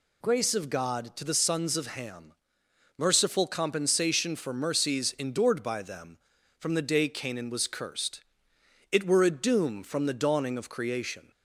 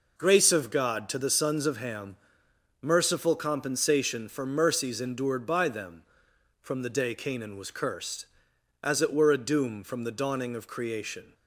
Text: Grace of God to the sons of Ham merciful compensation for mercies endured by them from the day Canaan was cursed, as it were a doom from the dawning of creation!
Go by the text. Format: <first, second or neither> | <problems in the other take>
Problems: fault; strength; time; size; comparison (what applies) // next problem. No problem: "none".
second | pauses between "Ham" and "merciful"; noticeable; at 2.3 s; 0.64 s long; noticeable in the second // skips "as"; at 8.5 s